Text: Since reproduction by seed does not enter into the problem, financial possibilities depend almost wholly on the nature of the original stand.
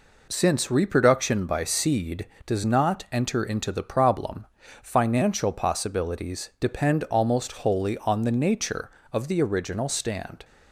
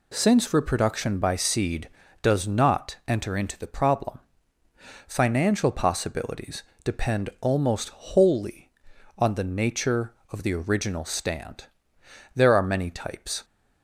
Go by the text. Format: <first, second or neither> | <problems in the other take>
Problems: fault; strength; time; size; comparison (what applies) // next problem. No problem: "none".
first | pauses between "possibilities" and "depend"; slight; at 6.6 s; 0.20 s long // goes on to say "There are many types"; noticeable; from 12.3 s on; 1.1 s long